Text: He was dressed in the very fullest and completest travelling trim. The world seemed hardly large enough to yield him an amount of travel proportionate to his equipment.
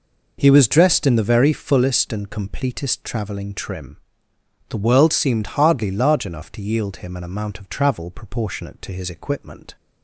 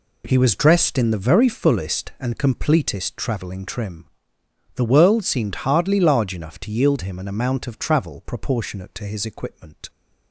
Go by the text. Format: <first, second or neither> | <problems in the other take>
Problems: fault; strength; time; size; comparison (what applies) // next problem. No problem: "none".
neither | none